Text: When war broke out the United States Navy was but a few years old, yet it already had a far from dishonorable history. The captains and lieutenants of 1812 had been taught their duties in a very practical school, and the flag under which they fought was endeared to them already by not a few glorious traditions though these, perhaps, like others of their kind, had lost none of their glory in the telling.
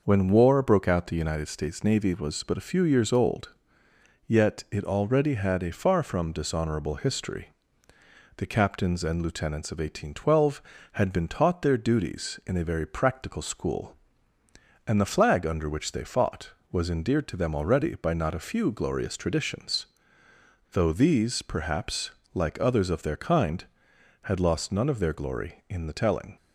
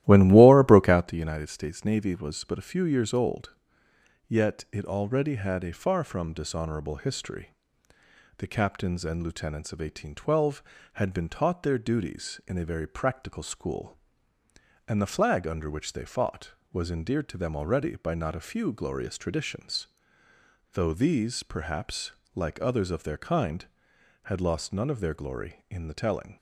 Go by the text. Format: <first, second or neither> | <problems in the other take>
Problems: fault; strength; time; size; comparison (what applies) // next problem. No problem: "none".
first | starts louder than the rest; strong; until 1.1 s; 14.5 dB // pauses between "traditions" and "though"; noticeable; at 19.8 s; 0.86 s long; noticeable in the first